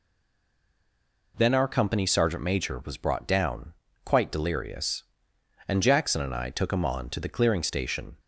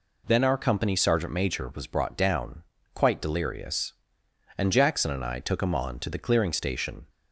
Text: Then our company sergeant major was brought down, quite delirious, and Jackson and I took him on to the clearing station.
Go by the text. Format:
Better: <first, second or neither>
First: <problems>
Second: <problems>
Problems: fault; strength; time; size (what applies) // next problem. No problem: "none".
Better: second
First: stays silent before the first word; noticeable; until 1.3 s; 1.3 s long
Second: none